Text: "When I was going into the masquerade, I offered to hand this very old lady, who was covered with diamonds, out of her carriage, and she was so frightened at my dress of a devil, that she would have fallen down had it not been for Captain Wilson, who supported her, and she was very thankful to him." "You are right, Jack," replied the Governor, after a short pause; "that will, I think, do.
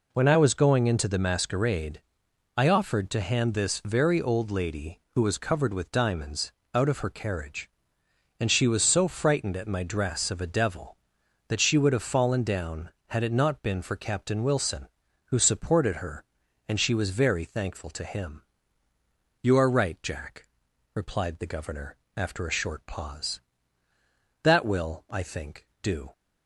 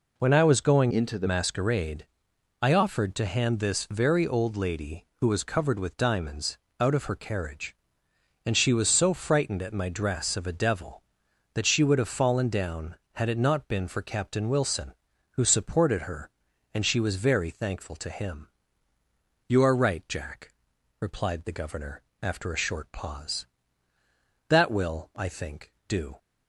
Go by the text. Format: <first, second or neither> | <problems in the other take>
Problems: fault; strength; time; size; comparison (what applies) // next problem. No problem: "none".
first | changes voice from "into" to "the"; from 0.9 to 1.2 s; 0.3 s long